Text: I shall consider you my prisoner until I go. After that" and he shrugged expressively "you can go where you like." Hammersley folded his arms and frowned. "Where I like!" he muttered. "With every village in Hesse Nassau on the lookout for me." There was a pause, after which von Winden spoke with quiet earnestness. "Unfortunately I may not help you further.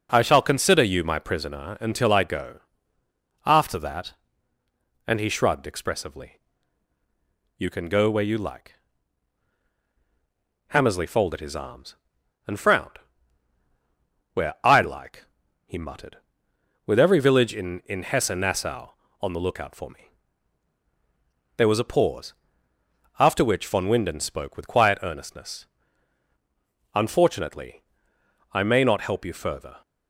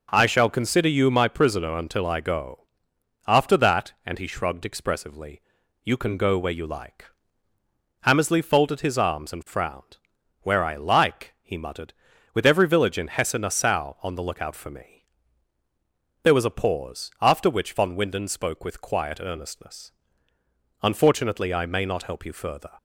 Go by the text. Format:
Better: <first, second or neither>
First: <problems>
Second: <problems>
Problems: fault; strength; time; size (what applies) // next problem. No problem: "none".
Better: second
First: pauses between "expressively" and "you"; at 6.4 s; 1.1 s long // says "in" twice; at 17.8 s // pauses between "Unfortunately" and "I"; noticeable; at 27.8 s; 0.70 s long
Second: pauses between "expressively" and "you"; at 5.4 s; 0.42 s long